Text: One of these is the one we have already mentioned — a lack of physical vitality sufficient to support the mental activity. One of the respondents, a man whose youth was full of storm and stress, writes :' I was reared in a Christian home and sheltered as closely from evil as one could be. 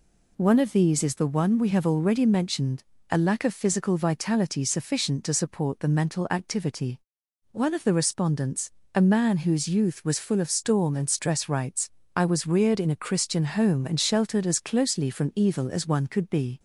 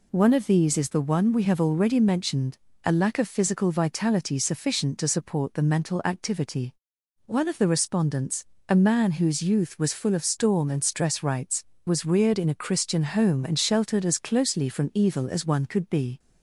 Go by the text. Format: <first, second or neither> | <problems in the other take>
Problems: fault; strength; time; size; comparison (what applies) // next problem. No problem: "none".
first | skips "I"; at 11.8 s